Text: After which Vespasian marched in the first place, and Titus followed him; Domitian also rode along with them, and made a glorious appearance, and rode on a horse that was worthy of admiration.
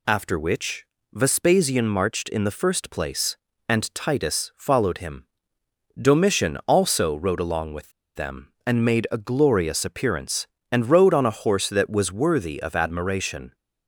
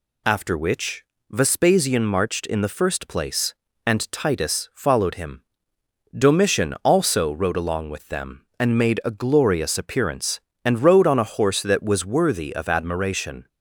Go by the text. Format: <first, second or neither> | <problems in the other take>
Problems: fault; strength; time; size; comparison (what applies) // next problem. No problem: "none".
second | pauses between "which" and "Vespasian"; slight; at 0.8 s; 0.28 s long; slight in the second // pauses between "with" and "them"; slight; at 7.9 s; 0.24 s long